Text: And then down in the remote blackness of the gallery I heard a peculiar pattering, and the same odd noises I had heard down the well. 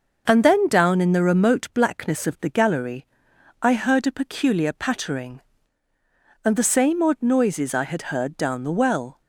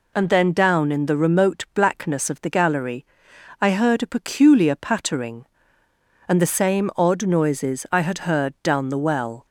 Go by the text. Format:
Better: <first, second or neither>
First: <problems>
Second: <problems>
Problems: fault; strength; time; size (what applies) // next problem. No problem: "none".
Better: neither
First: pauses between "gallery" and "I"; noticeable; at 3.0 s; 0.56 s long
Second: pauses between "gallery" and "I"; noticeable; at 3.0 s; 0.56 s long